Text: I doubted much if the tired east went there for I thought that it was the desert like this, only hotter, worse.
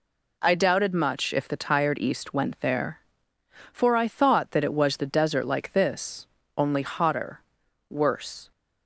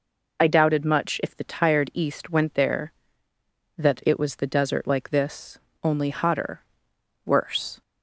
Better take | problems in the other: first | skips "for I thought"; at 3.3 s

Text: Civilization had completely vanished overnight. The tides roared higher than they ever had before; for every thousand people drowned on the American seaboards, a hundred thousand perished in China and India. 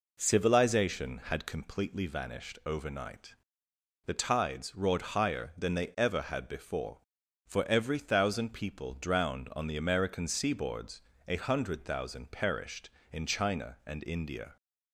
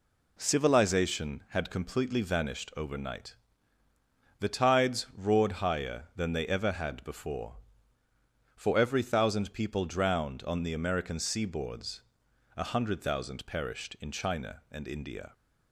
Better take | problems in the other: neither | none

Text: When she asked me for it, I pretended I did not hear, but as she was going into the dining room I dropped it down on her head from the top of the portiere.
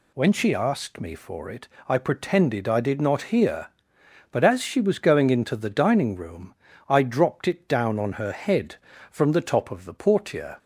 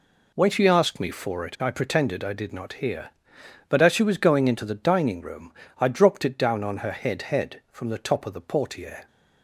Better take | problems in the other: first | pauses between "room" and "I"; slight; at 5.5 s; 0.30 s long; slight in the first // says "head" twice; at 7.2 s

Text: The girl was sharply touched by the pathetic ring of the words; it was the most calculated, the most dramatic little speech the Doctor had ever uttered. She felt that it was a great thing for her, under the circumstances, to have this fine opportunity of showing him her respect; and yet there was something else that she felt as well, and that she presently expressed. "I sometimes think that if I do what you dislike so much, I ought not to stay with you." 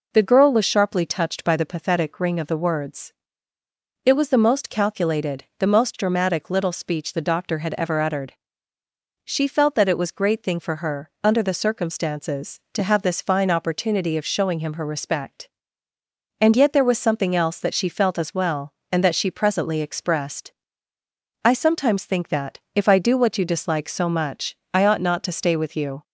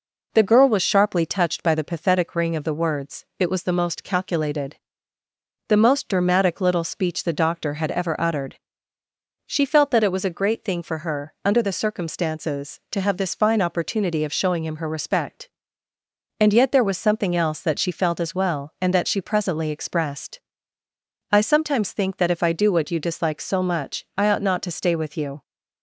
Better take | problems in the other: second | skips "a"; at 10.1 s // pauses between "that" and "if"; slight; at 22.5 s; 0.16 s long

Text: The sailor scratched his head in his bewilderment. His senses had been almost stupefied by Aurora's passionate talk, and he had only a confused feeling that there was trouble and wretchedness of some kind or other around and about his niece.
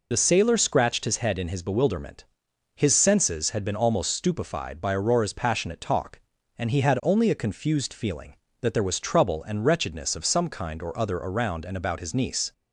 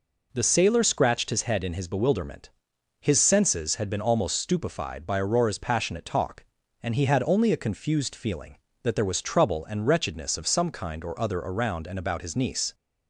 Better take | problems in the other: second | loses the start of "The"; at 0.1 s; 55 ms

